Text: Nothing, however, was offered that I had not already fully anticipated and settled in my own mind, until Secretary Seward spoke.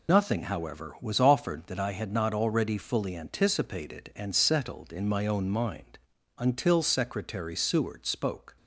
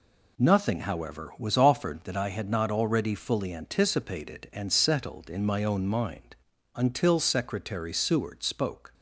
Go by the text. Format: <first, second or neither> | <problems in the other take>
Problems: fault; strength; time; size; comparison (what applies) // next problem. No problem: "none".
second | loses the start of "Nothing"; at 0.0 s; 90 ms